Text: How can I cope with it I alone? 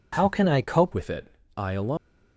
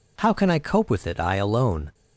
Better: second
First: changes voice at "with"; from 0.9 s on; 1.0 s long // pauses between "it" and "I"; slight; at 1.3 s; 0.24 s long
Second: none

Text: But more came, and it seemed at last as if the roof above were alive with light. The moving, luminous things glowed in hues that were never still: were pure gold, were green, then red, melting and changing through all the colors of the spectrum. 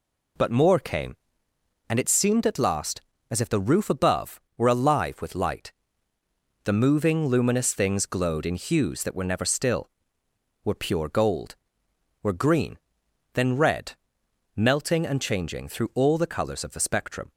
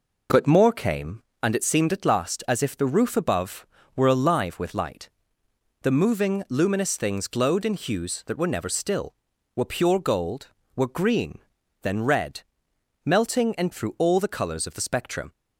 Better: first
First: none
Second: skips "changing"; at 13.7 s

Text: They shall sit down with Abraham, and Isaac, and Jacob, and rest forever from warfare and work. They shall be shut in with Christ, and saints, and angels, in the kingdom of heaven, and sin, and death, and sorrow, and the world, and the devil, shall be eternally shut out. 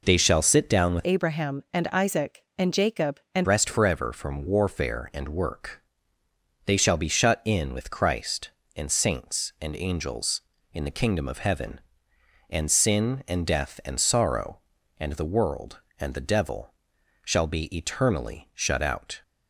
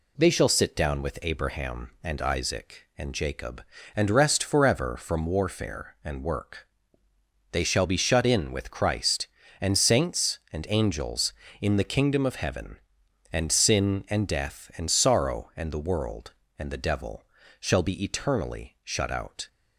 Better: second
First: changes voice from "Abraham" to "and"; from 1.0 to 3.4 s; 2.4 s long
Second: none

